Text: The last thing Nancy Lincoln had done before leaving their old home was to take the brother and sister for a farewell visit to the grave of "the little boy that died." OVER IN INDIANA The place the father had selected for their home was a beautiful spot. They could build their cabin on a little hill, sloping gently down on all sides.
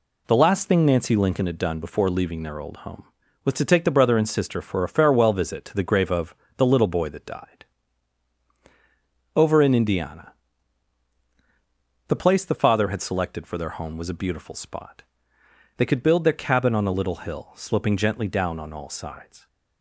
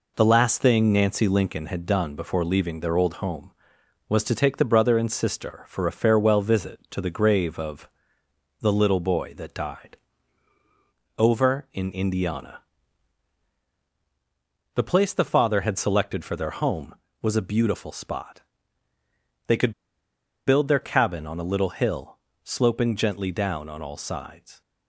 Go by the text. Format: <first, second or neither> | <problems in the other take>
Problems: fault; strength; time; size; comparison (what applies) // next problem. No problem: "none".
first | pauses between "of" and "the"; noticeable; at 7.8 s; 0.72 s long; slight in the first // pauses between "INDIANA" and "The"; strong; at 12.5 s; 2.1 s long; strong in the first // pauses between "could" and "build"; noticeable; at 19.7 s; 0.74 s long